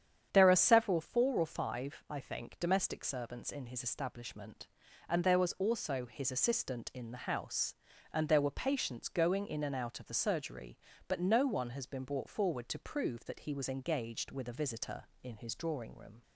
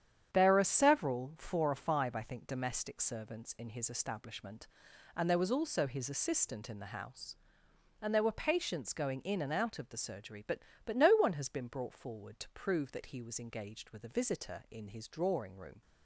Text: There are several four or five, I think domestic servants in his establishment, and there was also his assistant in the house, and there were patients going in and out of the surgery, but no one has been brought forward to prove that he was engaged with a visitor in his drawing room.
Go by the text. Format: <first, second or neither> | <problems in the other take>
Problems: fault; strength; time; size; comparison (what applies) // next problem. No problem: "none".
first | starts louder than the rest; strong; until 1.3 s; 9 dB; strong in the first // says "but" twice; at 10.8 s